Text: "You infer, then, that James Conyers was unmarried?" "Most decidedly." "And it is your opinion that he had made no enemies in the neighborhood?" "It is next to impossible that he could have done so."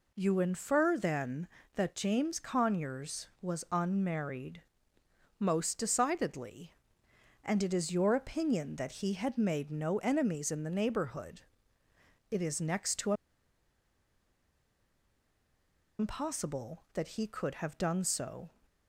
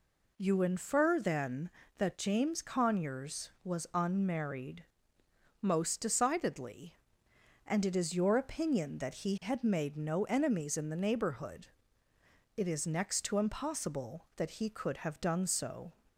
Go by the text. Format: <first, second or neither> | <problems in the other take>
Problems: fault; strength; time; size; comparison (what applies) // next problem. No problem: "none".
second | pauses between "to" and "impossible"; strong; at 13.1 s; 2.8 s long